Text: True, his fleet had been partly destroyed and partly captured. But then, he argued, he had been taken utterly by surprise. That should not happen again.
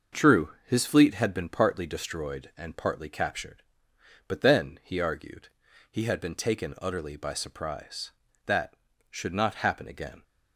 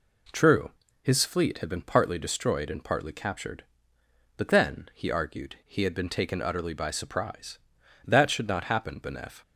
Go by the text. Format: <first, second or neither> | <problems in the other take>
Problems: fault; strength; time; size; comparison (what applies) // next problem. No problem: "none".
first | says "benef" for "again"; at 8.9 s